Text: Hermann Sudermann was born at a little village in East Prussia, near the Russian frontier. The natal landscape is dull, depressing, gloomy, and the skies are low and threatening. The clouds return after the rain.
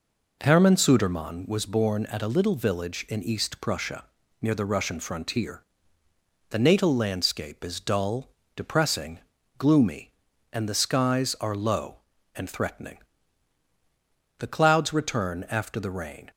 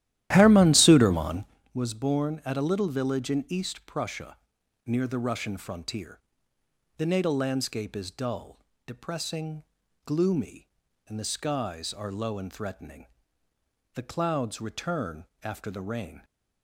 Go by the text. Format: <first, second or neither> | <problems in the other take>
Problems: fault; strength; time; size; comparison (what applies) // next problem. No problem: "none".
first | starts louder than the rest; strong; until 1.6 s; 13.5 dB // pauses between "return" and "after"; slight; at 15.2 s; 0.18 s long